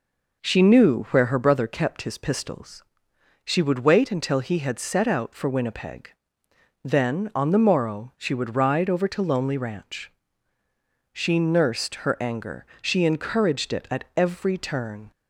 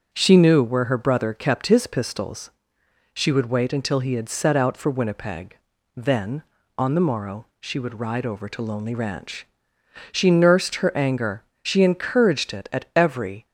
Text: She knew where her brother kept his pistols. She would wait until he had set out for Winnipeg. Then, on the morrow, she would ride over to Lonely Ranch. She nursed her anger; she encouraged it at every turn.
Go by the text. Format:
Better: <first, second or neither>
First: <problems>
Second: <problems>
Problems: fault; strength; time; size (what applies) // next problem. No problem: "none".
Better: first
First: none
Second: starts louder than the rest; until 1.1 s; 7 dB // stops before "turn"; at 13.4 s